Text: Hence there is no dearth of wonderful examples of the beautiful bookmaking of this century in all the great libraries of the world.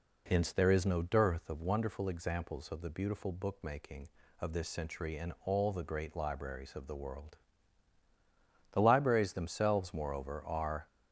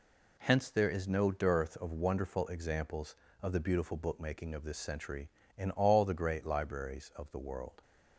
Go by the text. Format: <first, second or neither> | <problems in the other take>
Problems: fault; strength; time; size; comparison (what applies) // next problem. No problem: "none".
second | goes on to say "The libraries themselves moreover are"; strong; from 8.7 s on; 2.1 s long